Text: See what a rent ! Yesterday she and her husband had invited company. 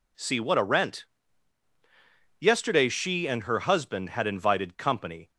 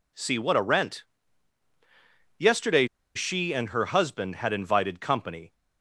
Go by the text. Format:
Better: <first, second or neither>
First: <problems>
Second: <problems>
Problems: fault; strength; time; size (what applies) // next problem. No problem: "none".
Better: first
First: none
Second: pauses between "Yesterday" and "she"; slight; at 2.8 s; 0.30 s long